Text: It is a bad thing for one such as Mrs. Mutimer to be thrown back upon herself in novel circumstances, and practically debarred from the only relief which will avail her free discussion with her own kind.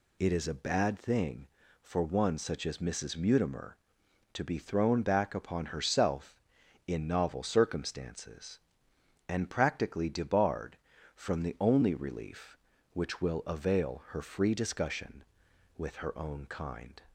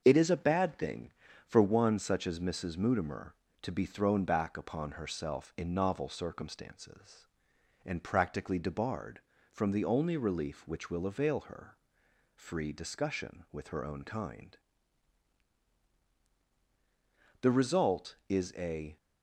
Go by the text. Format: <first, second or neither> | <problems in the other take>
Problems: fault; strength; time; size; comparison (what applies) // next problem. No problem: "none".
first | starts louder than the rest; until 1.0 s; 6.5 dB // pauses between "her" and "free"; noticeable; at 11.7 s; 0.58 s long // goes on to say "The result is a"; from 17.4 s on; 1.5 s long